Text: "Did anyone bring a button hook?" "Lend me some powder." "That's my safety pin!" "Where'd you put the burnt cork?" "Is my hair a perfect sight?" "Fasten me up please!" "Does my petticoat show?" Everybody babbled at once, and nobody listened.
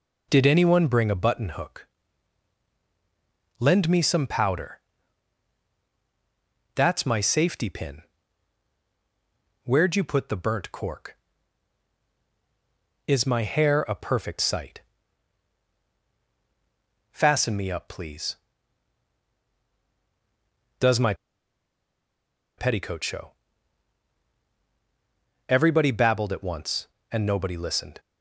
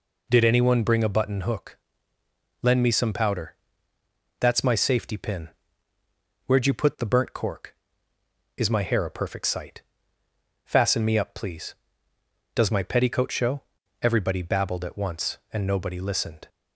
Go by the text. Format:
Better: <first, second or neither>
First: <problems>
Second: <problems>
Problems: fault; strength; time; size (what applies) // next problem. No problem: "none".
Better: second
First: pauses between "my" and "petticoat"; strong; at 21.1 s; 1.4 s long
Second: none